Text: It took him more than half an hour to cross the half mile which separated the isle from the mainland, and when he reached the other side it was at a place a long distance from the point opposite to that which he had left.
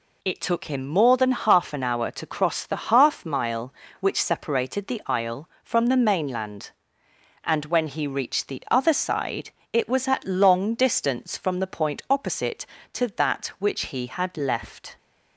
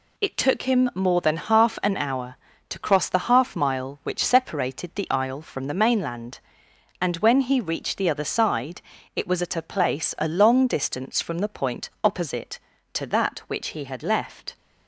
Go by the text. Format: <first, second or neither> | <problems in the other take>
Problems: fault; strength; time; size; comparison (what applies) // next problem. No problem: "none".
second | pauses between "side" and "it"; slight; at 9.4 s; 0.24 s long; slight in the second // skips "a place a"; at 10.2 s